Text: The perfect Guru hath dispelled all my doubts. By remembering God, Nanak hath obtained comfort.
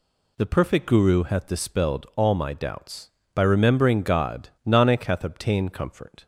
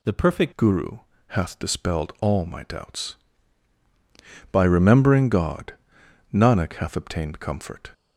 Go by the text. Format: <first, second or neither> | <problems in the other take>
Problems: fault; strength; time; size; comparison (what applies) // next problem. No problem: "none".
first | changes voice at "Guru"; from 0.5 s on; 7.4 s long // pauses between "Guru" and "hath"; slight; at 0.9 s; 0.28 s long